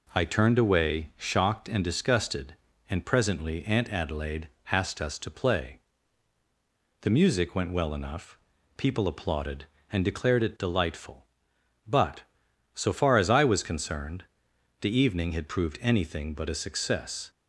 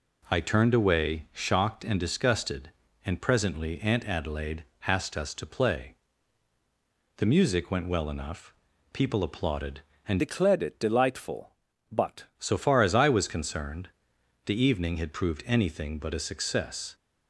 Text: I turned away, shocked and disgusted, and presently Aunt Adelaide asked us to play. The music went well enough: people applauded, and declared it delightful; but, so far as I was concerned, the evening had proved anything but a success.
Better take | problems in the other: first | pauses between "Adelaide" and "asked"; slight; at 4.6 s; 0.24 s long; slight in the first // changes voice from "declared" to "but"; from 10.1 to 12.2 s; 2.1 s long

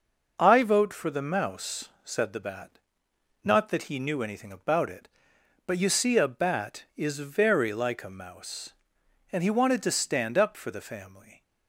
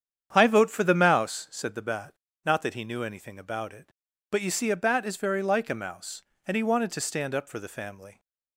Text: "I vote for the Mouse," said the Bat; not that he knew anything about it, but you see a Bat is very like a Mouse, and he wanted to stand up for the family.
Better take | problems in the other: first | starts louder than the rest; strong; until 1.3 s; 8.5 dB

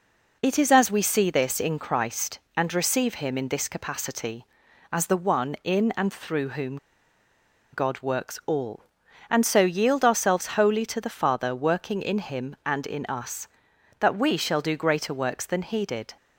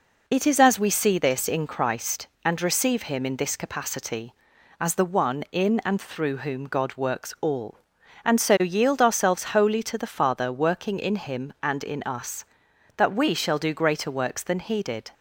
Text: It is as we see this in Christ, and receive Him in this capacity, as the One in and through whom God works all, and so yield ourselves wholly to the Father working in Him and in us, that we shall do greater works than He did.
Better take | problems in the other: second | pauses between "whom" and "God"; noticeable; at 6.7 s; 0.96 s long

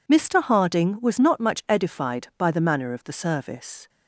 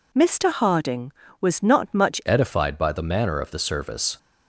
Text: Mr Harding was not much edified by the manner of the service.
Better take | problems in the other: first | changes voice at "edified"; from 2.2 s on; 1.9 s long

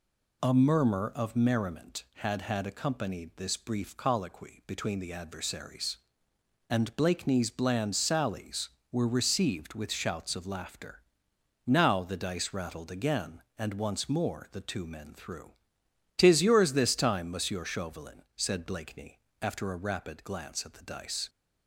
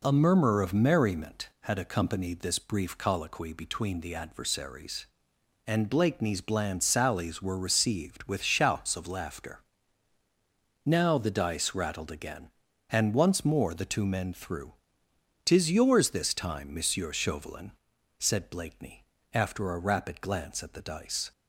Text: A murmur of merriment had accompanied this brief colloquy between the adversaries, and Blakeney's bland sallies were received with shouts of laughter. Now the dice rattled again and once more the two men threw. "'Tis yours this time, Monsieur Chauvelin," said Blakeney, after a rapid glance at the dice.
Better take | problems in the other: second | says "had" twice; at 2.4 s

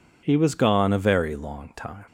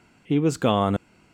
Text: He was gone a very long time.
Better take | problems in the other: first | stops before "a very long time"; at 0.9 s

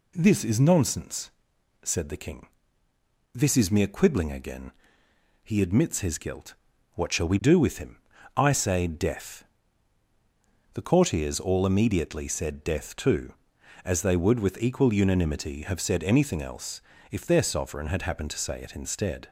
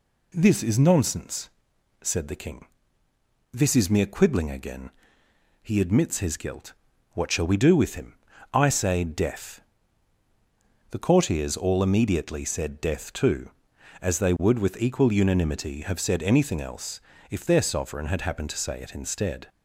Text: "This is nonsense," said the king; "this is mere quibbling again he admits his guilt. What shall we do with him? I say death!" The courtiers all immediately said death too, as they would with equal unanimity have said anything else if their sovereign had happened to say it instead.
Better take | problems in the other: neither | pauses between "again" and "he"; noticeable; the same in both // pauses between "else" and "if"; slight; the same in both

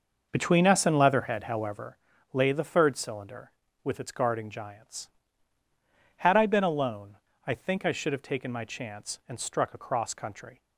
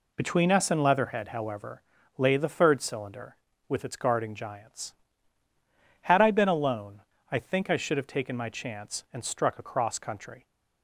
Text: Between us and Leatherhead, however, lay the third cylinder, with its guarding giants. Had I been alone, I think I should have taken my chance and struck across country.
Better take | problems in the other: second | starts louder than the rest; noticeable; until 1.9 s; 6 dB

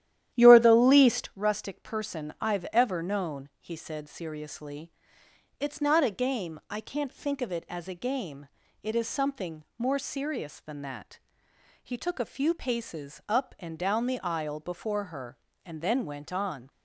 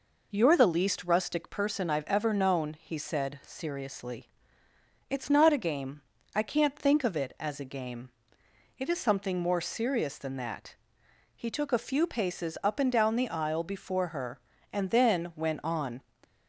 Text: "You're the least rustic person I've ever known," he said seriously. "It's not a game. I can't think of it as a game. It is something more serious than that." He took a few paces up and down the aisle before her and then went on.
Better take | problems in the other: second | starts louder than the rest; strong; until 1.4 s; 11.5 dB

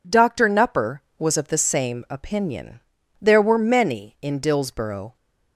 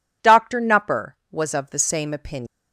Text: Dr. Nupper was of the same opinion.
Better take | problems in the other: second | goes on to say "There were many in Dillsborough"; strong; from 3.1 s on; 1.9 s long

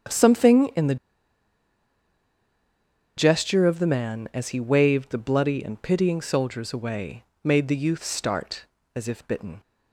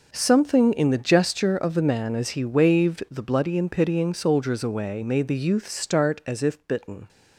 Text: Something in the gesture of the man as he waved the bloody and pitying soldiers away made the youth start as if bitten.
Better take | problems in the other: second | starts louder than the rest; strong; until 3.3 s; 8.5 dB // pauses between "the" and "gesture"; strong; at 0.9 s; 2.2 s long // pauses between "away" and "made"; slight; at 7.2 s; 0.22 s long

